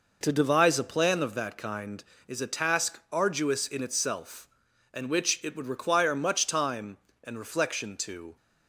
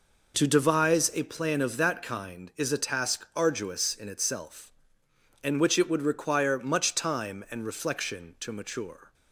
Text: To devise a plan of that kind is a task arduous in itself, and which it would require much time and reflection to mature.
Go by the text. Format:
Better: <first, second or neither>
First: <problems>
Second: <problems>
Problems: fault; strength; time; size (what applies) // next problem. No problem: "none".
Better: second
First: stops before "mature"; at 8.3 s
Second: none